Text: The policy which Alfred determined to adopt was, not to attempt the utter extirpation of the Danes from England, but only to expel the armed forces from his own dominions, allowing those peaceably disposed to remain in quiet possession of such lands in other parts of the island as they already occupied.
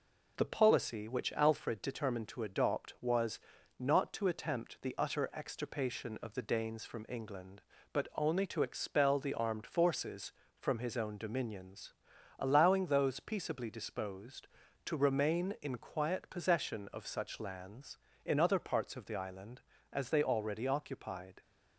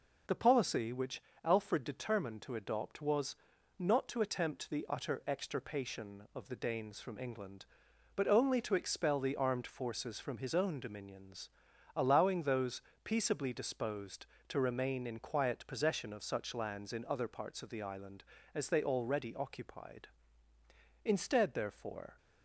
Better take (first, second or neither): first